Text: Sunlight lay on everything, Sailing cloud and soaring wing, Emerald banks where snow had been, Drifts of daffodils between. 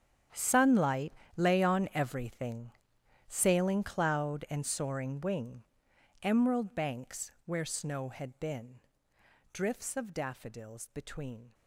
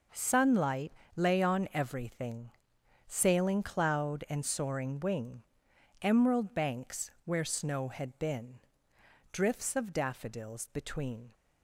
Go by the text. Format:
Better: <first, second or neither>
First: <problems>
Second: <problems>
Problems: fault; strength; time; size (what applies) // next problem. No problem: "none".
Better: second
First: gets quieter; strong; throughout; 16.5 dB // pauses between "Sunlight" and "lay"; slight; at 1.1 s; 0.24 s long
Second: pauses between "Sunlight" and "lay"; slight; at 0.9 s; 0.24 s long